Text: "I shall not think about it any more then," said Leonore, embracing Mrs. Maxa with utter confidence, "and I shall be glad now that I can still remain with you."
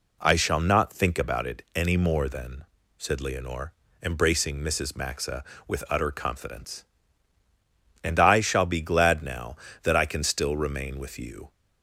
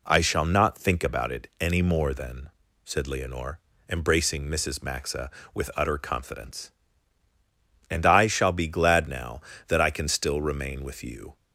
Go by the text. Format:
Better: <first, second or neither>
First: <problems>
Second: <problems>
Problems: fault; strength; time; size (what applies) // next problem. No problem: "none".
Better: neither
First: none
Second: none